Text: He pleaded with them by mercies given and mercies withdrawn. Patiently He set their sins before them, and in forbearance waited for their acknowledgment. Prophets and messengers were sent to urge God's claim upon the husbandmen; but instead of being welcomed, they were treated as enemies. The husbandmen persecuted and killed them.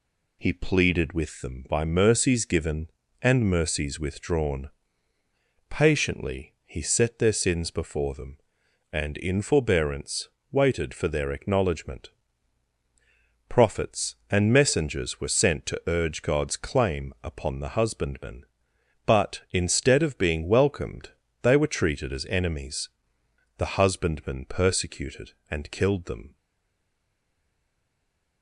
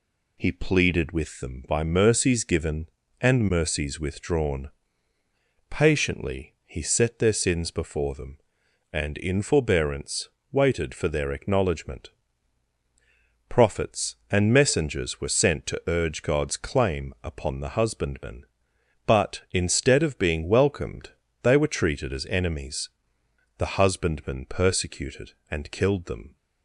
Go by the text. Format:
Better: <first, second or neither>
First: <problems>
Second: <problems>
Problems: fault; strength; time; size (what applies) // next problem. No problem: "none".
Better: second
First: pauses between "forbearance" and "waited"; slight; at 10.2 s; 0.22 s long // stays silent after the last word; noticeable; from 26.3 s on; 2.1 s long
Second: pauses between "forbearance" and "waited"; slight; at 10.2 s; 0.22 s long